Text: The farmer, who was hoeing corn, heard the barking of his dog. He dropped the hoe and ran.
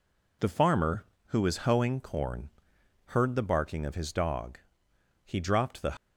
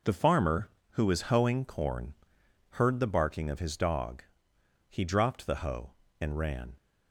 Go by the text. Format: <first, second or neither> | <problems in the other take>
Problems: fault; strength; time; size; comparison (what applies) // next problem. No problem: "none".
second | stops before "hoe and ran"; at 5.9 s